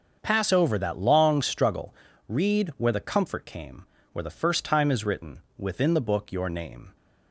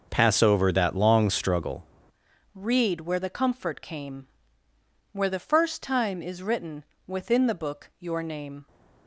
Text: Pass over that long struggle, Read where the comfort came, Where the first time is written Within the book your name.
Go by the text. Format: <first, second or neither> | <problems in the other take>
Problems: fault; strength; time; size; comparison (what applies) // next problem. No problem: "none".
first | starts louder than the rest; until 1.1 s; 6.5 dB; also in the first // changes voice at "Read"; from 2.5 s on; 6.1 s long // pauses between "written" and "Within"; slight; at 6.8 s; 0.22 s long; slight in the first